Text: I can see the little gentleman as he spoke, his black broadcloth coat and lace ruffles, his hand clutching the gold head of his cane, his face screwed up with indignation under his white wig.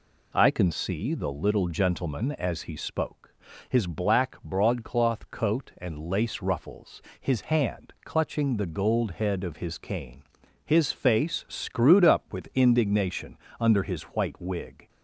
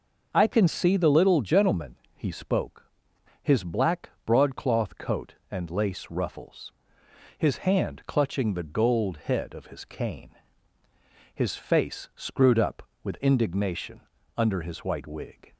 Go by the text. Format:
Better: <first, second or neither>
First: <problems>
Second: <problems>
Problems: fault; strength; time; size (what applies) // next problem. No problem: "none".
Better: first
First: pauses between "indignation" and "under"; slight; at 13.3 s; 0.24 s long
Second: skips "as"; at 2.0 s // pauses between "black" and "broadcloth"; slight; at 4.0 s; 0.16 s long // pauses between "indignation" and "under"; slight; at 14.0 s; 0.36 s long